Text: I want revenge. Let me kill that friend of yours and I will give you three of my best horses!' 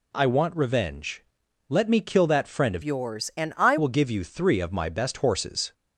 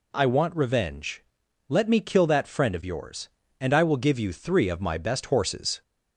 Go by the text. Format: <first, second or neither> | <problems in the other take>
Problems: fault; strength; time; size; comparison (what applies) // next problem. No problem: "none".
second | changes voice from "yours" to "I"; from 2.8 to 3.7 s; 0.9 s long